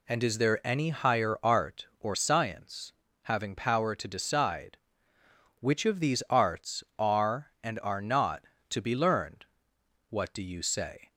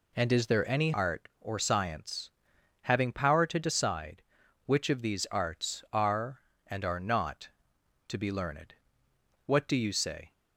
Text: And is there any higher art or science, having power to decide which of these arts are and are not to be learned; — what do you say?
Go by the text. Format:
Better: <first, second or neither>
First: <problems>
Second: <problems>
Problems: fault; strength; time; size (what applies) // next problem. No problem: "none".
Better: first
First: none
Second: skips "higher"; at 0.9 s